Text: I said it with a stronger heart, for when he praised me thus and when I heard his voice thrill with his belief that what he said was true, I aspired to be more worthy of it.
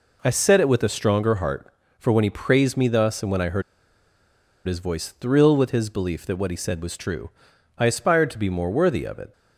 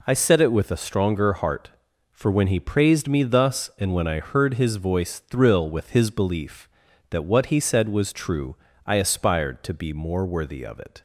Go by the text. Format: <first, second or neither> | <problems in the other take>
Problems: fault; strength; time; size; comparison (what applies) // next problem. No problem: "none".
second | pauses between "heard" and "his"; at 3.6 s; 1.0 s long